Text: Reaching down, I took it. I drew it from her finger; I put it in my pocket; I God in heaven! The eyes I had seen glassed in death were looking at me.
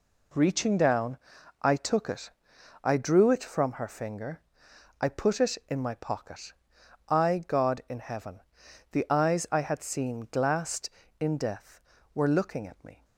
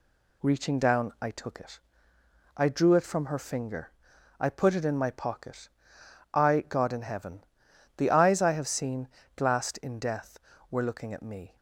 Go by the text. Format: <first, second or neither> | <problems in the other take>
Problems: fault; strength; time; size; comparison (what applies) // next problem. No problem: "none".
first | says "have" for "had"; at 8.5 s // pauses between "seen" and "glassed"; slight; at 9.0 s; 0.26 s long